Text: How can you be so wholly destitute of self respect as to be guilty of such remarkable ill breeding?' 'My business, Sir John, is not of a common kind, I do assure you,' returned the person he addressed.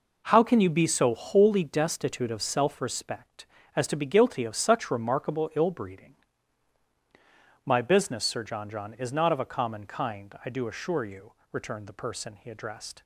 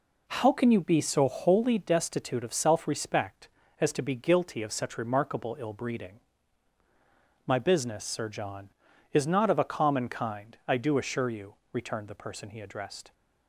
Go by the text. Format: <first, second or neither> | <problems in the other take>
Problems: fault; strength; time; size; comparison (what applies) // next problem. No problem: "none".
second | says "John" twice; at 8.7 s